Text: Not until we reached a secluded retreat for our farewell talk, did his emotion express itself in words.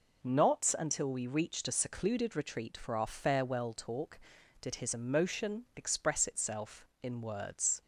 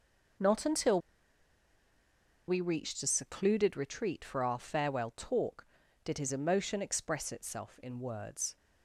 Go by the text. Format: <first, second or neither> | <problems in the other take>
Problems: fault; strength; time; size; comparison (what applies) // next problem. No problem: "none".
first | pauses between "until" and "we"; strong; at 1.0 s; 1.4 s long